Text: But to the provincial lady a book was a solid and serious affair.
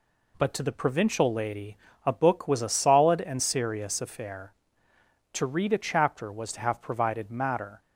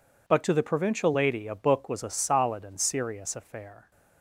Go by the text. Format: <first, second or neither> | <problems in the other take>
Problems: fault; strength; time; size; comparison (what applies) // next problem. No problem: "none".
second | pauses between "lady" and "a"; slight; at 1.7 s; 0.28 s long // goes on to say "To read a chapter was to have provided matter"; strong; from 5.3 s on; 2.4 s long